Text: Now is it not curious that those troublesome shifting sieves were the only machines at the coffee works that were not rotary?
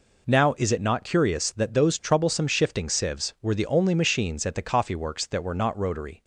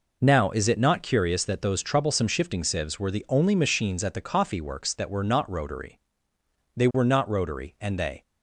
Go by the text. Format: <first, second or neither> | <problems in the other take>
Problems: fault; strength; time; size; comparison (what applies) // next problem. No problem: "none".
first | goes on to say "They were not rotary and they"; from 6.7 s on; 1.4 s long